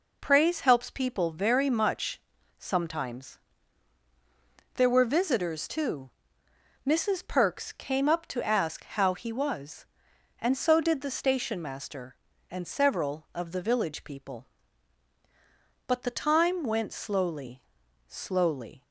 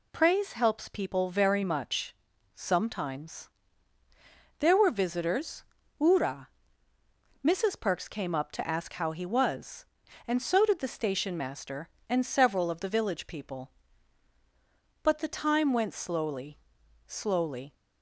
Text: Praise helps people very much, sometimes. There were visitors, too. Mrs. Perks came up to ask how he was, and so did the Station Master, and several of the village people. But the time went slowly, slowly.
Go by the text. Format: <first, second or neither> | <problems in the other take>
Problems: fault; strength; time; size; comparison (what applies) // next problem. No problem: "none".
first | says "ura" for "too"; at 5.9 s